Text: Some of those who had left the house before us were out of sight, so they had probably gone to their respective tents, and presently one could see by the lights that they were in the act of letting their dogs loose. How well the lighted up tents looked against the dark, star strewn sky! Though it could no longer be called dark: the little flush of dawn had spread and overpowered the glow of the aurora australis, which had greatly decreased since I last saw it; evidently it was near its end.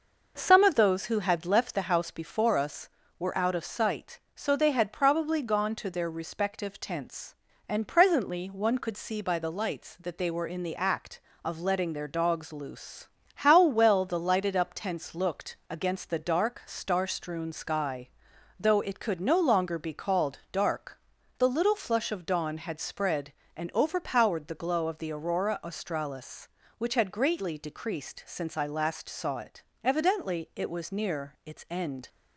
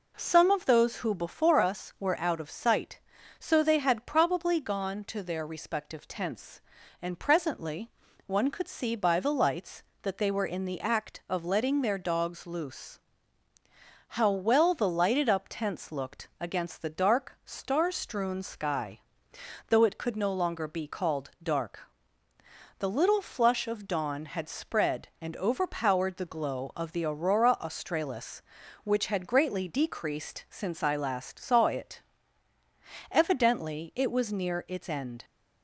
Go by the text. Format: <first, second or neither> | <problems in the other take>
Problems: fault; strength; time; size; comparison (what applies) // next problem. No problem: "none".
first | skips "had left the house"; at 1.1 s // pauses between "presently" and "one"; slight; at 7.9 s; 0.36 s long